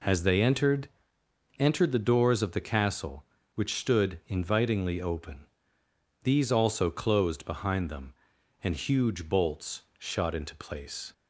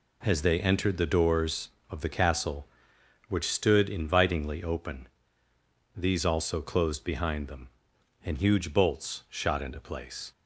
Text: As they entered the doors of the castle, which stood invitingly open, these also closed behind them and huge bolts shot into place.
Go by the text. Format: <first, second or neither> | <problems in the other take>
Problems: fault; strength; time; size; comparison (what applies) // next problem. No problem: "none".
second | says "entered" twice; at 1.6 s // pauses between "bolts" and "shot"; slight; at 9.8 s; 0.16 s long